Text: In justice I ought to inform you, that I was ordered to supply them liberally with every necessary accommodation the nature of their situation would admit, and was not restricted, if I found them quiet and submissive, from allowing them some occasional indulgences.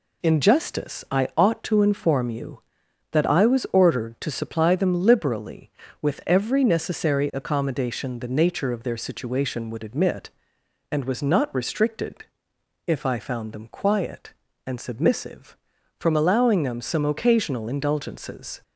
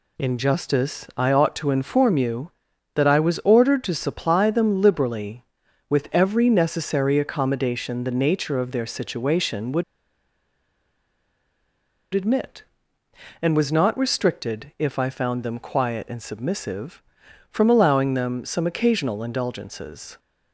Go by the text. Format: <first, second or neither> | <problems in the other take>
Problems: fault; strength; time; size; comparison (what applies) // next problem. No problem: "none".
first | pauses between "would" and "admit"; strong; at 9.8 s; 2.3 s long